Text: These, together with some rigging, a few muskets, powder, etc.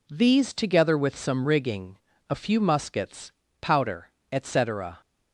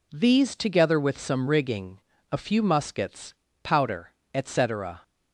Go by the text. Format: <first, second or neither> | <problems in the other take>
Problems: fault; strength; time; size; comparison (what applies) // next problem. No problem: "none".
neither | none